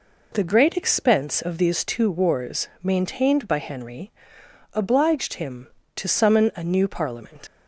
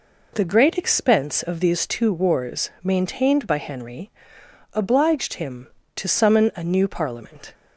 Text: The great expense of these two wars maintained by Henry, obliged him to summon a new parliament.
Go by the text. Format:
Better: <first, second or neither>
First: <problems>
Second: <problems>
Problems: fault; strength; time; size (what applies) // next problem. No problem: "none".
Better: second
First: leaves "parliament" unfinished; at 7.4 s; 60 ms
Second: none